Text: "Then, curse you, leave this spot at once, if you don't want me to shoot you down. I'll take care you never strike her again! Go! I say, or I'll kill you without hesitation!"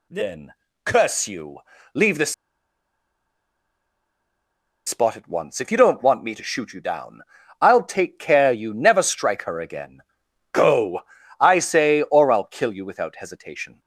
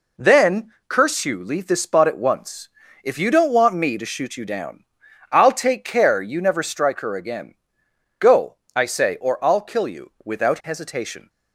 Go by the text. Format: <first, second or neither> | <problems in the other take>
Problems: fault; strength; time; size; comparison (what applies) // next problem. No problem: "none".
second | pauses between "this" and "spot"; strong; at 2.3 s; 2.5 s long